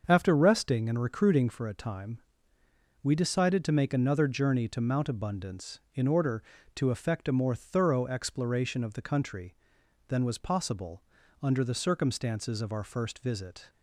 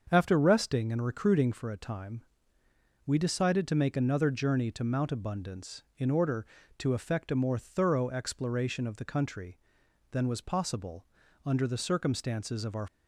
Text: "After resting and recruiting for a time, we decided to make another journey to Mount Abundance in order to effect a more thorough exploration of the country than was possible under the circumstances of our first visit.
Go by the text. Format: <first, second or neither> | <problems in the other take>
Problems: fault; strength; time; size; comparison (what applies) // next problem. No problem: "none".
first | starts louder than the rest; until 1.1 s; 6.5 dB; also in the first // pauses between "possible" and "under"; at 11.0 s; 0.38 s long; also in the first // stops before "first visit"; at 12.8 s